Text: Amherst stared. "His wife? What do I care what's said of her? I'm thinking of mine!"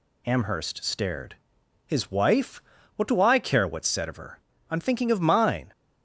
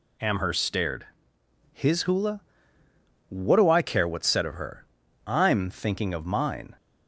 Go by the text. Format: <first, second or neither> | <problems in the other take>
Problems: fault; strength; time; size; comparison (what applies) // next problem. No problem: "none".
first | says "hula" for "wife"; at 2.0 s